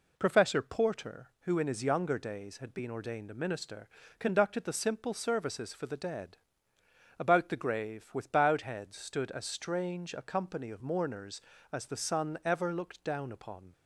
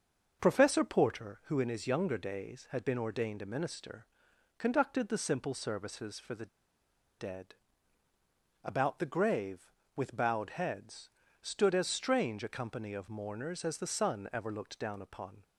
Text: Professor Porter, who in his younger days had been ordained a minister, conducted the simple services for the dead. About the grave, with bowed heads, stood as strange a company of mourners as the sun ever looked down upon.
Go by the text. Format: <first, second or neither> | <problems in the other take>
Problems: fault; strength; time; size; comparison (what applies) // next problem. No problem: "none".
first | starts louder than the rest; until 1.4 s; 6.5 dB // pauses between "the" and "dead"; noticeable; at 6.4 s; 0.72 s long